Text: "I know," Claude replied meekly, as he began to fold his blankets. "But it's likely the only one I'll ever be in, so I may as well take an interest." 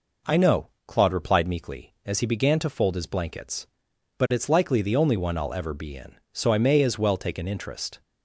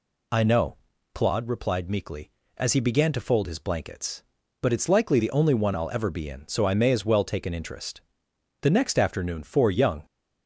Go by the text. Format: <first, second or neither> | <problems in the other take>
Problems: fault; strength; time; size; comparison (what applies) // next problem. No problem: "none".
first | goes on to say "The next afternoon four young"; from 8.6 s on; 1.4 s long